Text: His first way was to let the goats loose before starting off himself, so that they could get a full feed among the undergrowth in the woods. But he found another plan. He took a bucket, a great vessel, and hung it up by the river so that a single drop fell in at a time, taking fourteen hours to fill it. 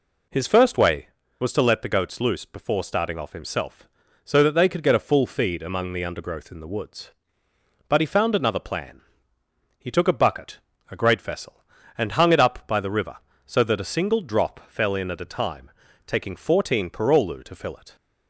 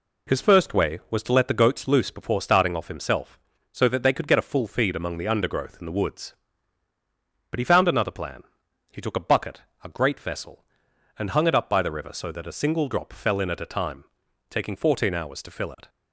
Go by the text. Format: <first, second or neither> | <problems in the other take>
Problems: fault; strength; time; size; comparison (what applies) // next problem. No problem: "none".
second | says "parolu" for "hours"; at 16.8 s